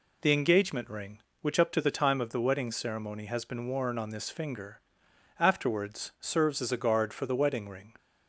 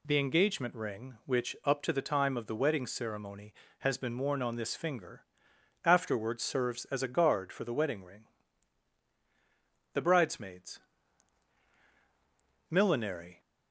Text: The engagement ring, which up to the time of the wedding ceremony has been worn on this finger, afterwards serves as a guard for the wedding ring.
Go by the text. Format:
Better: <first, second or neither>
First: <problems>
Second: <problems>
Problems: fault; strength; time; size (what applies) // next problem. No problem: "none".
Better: first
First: none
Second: goes on to say "The Bridesmaids Millinery"; strong; from 9.9 s on; 3.4 s long